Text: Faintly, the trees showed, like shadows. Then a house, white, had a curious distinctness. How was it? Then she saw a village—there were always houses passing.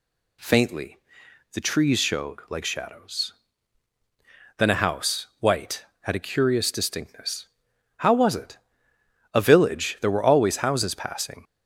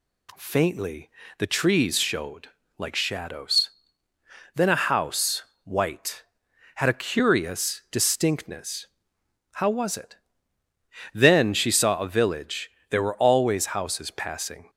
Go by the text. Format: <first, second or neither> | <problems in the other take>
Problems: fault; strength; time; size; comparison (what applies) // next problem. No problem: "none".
second | skips "Then she saw"; at 8.9 s